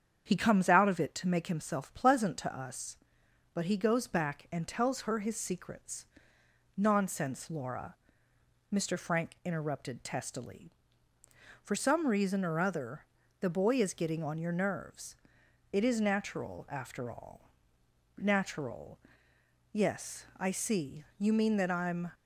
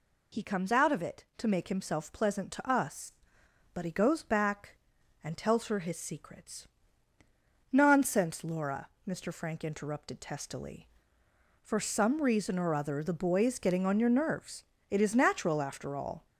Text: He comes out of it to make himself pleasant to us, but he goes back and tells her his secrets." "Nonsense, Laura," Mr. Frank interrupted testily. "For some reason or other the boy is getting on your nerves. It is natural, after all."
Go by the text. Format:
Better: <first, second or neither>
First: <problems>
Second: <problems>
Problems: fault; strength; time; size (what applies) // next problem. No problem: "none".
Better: second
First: starts louder than the rest; strong; until 1.2 s; 8 dB // pauses between "other" and "the"; slight; at 13.0 s; 0.34 s long // goes on to say "Natural Yes I see you mean that I'm"; strong; from 18.1 s on; 3.9 s long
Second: none